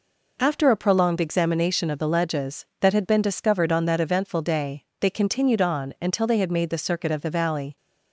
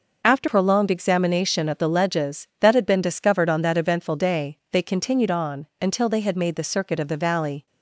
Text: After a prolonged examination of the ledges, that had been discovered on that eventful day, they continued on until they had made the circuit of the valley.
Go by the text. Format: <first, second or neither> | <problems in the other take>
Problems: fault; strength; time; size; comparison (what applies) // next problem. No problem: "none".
first | skips "a"; at 0.4 s // pauses between "on" and "until"; slight; at 5.6 s; 0.16 s long